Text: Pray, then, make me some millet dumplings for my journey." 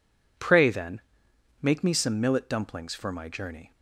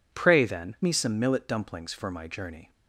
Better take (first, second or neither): first